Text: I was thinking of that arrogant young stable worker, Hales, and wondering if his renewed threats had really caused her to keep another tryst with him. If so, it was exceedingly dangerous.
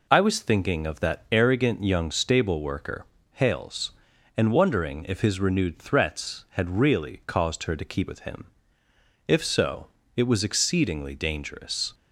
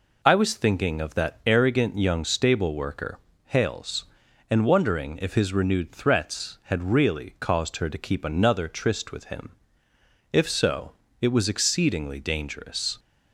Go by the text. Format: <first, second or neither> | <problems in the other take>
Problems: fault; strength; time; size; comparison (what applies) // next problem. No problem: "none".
second | skips "another tryst"; at 8.0 s